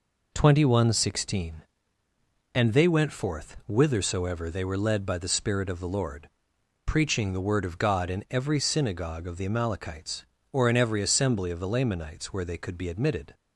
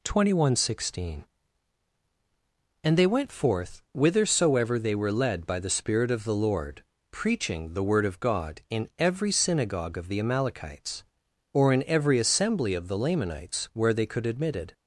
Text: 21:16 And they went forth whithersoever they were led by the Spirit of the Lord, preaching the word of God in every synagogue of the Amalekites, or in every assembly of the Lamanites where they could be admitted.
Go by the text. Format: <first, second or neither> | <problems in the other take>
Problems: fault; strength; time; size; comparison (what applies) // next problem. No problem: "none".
first | skips "be"; at 14.2 s